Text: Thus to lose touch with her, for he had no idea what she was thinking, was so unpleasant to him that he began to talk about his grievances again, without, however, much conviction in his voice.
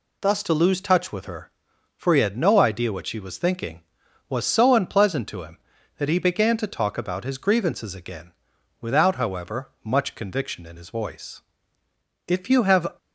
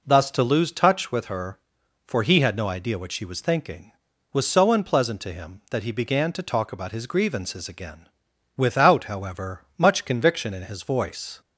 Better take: second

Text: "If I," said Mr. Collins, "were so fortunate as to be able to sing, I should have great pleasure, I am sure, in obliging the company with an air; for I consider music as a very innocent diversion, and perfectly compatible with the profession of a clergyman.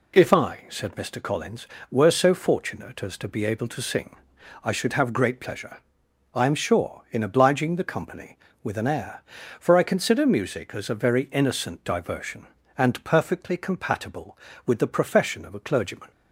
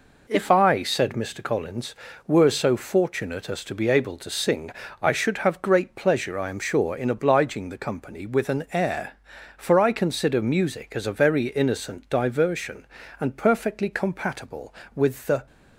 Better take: first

